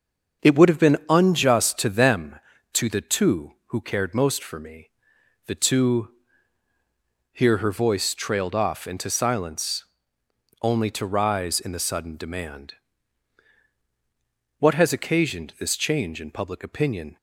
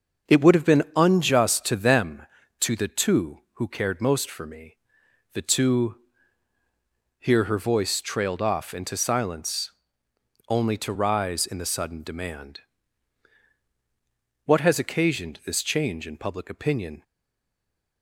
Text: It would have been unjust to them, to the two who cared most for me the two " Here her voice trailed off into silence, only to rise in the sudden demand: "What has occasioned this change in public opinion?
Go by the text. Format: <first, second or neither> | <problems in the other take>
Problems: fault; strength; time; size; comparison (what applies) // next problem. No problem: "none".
first | starts louder than the rest; strong; until 1.4 s; 7.5 dB; strong in the first // pauses between "me" and "the"; noticeable; at 4.7 s; 0.56 s long; noticeable in the first // stays silent after the last word; from 17.0 s on; 1.0 s long